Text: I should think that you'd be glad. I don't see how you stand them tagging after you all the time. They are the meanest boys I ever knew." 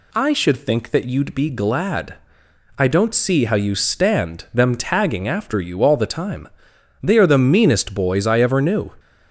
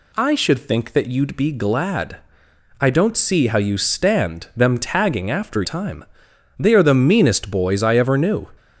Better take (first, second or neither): first